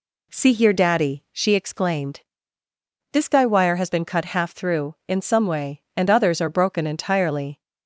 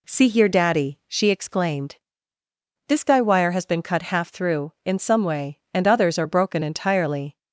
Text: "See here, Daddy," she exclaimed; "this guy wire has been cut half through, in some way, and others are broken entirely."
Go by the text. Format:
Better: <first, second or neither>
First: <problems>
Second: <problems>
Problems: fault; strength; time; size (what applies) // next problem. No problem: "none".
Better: neither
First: none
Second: none